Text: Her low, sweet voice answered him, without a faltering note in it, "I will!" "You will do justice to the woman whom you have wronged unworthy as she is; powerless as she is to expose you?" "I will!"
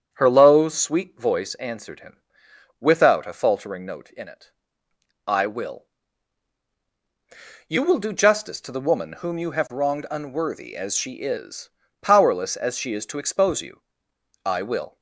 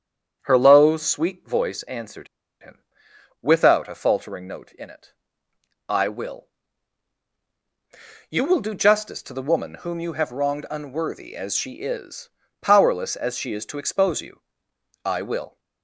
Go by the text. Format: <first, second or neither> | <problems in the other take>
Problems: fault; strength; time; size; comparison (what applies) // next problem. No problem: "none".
first | starts louder than the rest; strong; until 1.4 s; 8 dB; strong in the first // pauses between "answered" and "him"; slight; at 2.2 s; 0.35 s long